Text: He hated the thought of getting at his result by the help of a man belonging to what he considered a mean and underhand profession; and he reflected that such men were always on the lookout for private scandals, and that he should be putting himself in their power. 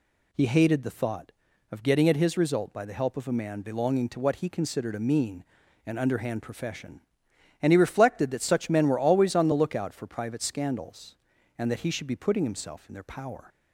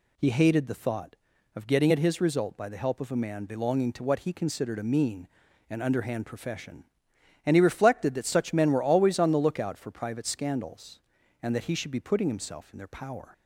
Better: neither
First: none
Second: none

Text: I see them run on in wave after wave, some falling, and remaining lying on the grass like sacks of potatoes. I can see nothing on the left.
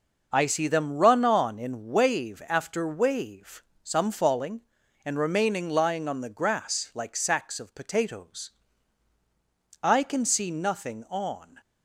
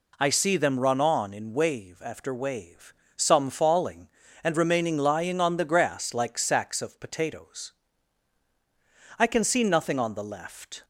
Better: second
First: stops before "the left"; at 11.6 s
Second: none

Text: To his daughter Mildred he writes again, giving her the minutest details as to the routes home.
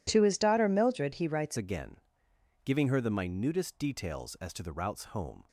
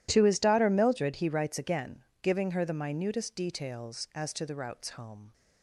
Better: second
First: changes voice at "again"; from 1.5 s on; 3.9 s long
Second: none

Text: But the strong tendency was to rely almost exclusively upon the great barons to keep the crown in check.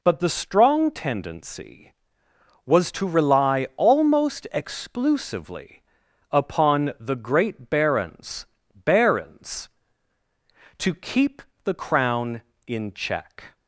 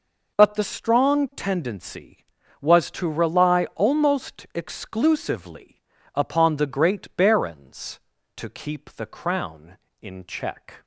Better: second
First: pauses between "exclusively" and "upon"; noticeable; at 5.8 s; 0.48 s long // says "barons" twice; at 8.7 s // pauses between "keep" and "the"; slight; at 11.4 s; 0.22 s long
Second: pauses between "exclusively" and "upon"; slight; at 5.8 s; 0.32 s long

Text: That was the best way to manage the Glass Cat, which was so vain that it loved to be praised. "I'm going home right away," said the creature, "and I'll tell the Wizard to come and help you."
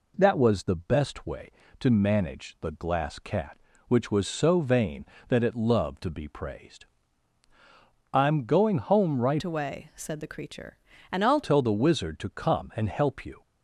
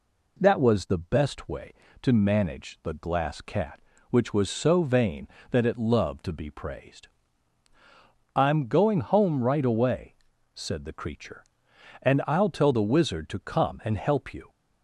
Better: second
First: changes voice from "away" to "I'll"; from 9.4 to 11.4 s; 2.0 s long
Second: none

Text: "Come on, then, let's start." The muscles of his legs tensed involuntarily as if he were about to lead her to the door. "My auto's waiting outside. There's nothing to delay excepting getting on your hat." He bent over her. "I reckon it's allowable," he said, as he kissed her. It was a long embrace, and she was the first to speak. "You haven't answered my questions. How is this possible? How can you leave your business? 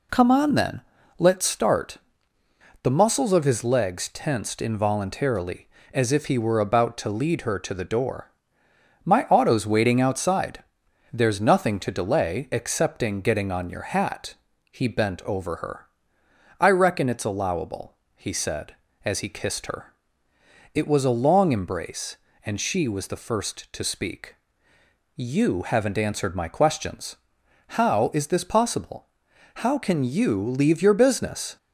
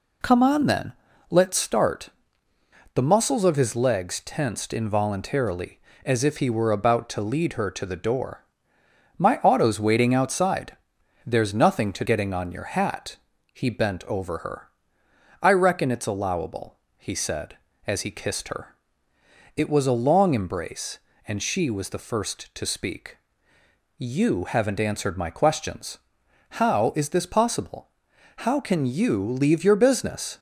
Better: first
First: none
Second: skips "delay excepting"; at 12.0 s

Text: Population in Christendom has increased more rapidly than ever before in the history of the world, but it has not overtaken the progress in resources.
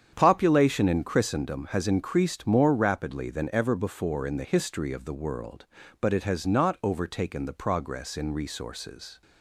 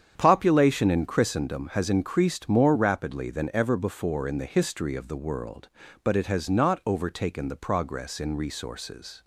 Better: neither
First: starts louder than the rest; strong; until 1.1 s; 8.5 dB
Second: starts louder than the rest; strong; until 1.1 s; 8.5 dB

